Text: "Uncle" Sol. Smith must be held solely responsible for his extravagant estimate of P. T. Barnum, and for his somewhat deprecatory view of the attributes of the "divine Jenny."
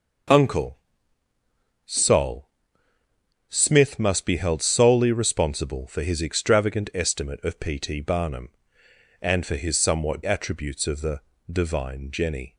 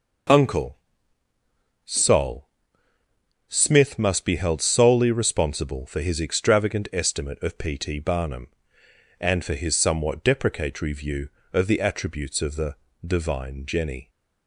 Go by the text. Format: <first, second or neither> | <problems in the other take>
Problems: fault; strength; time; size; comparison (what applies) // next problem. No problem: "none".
second | pauses between "Uncle" and "Sol"; at 0.7 s; 1.1 s long; also in the second // skips "deprecatory view of the"; at 10.2 s // pauses between "the" and "divine"; slight; at 11.2 s; 0.30 s long; slight in the second